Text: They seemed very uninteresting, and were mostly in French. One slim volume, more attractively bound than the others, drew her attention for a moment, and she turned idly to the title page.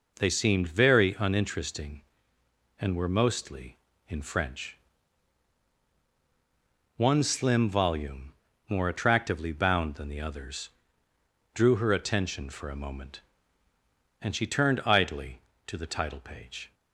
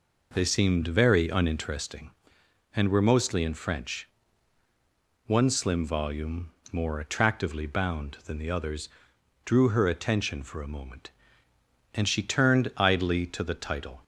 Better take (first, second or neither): first